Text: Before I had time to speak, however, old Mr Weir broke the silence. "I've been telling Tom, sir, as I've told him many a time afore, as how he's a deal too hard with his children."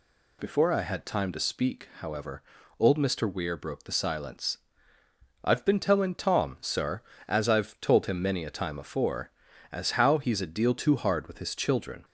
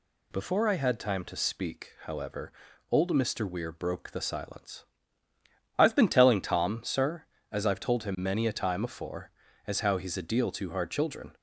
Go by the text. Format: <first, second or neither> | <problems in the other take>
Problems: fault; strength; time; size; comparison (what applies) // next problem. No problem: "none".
first | skips "with his"; at 10.8 s